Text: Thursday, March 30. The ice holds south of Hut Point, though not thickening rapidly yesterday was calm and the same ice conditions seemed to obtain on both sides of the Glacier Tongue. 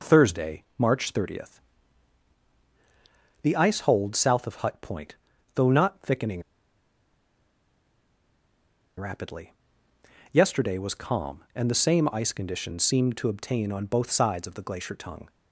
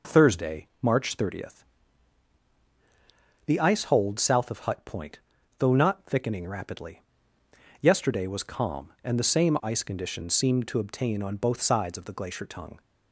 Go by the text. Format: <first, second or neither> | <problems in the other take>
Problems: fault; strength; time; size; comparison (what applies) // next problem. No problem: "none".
second | pauses between "thickening" and "rapidly"; strong; at 6.4 s; 2.5 s long // pauses between "rapidly" and "yesterday"; noticeable; at 9.5 s; 0.80 s long; noticeable in the second